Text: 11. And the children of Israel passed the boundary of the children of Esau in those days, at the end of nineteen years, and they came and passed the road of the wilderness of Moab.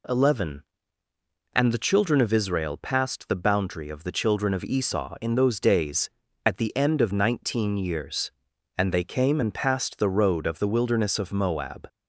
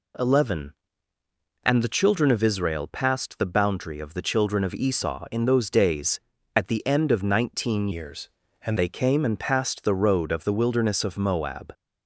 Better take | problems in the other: first | changes voice from "years" to "and"; from 7.9 to 8.7 s; 0.8 s long

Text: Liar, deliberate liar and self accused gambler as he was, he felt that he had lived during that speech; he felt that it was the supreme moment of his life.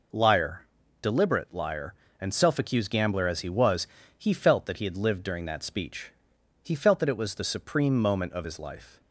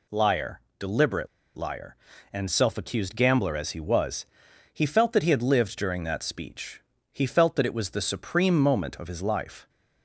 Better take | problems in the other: first | pauses between "deliberate" and "liar"; slight; at 1.2 s; 0.28 s long

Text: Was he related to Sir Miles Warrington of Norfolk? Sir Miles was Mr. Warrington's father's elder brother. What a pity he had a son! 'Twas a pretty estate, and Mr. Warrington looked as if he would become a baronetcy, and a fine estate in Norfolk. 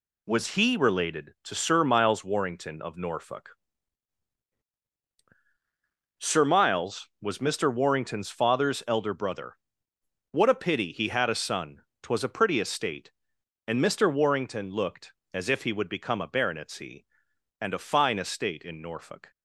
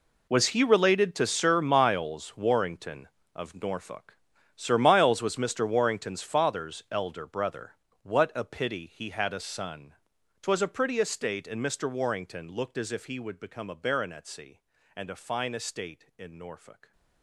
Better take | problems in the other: first | gets quieter; strong; throughout; 15.5 dB

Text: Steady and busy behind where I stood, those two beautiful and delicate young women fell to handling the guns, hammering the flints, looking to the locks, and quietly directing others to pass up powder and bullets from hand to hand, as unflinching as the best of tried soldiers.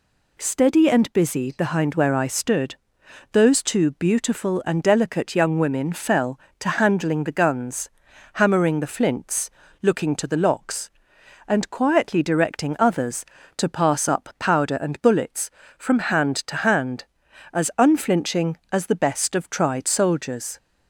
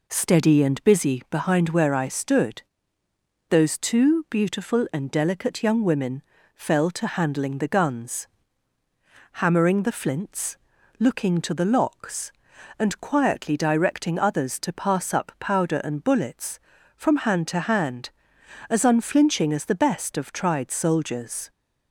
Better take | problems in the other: first | starts louder than the rest; until 1.1 s; 3.5 dB // pauses between "women" and "fell"; slight; at 6.2 s; 0.32 s long

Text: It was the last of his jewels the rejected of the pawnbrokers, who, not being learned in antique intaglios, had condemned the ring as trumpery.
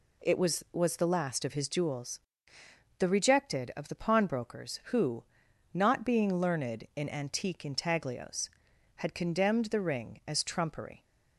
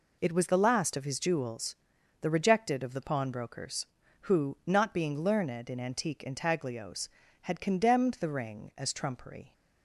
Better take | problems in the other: second | says "was" twice; at 0.7 s // pauses between "jewels" and "the"; noticeable; at 2.1 s; 0.80 s long; noticeable in the second

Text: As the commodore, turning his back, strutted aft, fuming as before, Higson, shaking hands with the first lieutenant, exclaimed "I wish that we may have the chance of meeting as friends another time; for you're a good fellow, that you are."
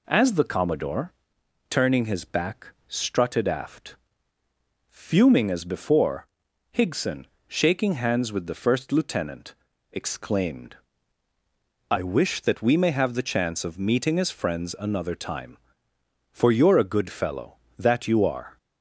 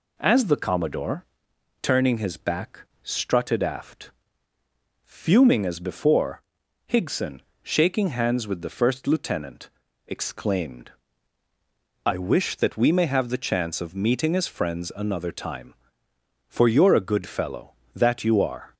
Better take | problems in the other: neither | pauses between "exclaimed" and "I"; the same in both

